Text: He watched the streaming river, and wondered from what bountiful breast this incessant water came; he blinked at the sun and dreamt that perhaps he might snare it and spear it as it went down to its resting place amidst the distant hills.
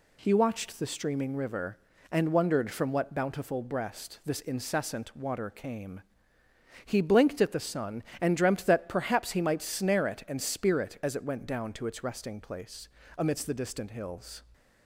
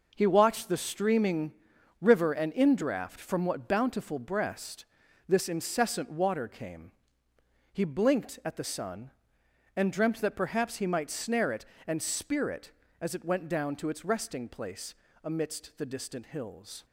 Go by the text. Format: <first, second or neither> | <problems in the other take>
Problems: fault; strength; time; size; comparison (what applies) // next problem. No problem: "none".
first | pauses between "streaming" and "river"; noticeable; at 1.5 s; 0.48 s long // says "indraft" for "wondered"; at 2.5 s // pauses between "breast" and "this"; at 4.8 s; 0.44 s long // pauses between "place" and "amidst"; slight; at 14.9 s; 0.30 s long; slight in the first